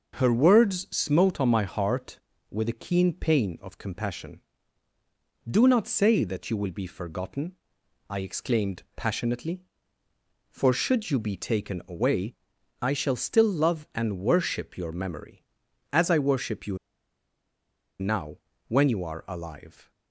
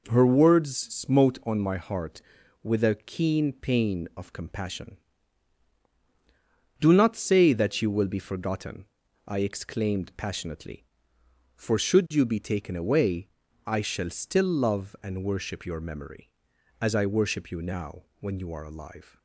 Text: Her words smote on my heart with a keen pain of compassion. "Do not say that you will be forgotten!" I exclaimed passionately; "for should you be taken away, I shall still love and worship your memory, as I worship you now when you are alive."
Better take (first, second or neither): second